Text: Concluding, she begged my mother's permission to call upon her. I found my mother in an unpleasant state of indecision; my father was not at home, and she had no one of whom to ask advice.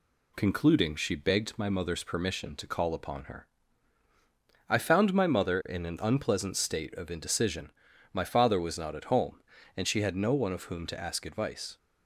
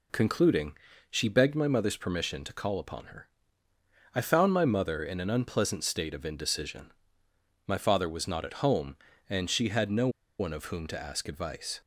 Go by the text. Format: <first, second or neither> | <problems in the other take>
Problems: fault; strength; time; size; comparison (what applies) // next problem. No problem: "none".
first | pauses between "no" and "one"; slight; at 10.0 s; 0.30 s long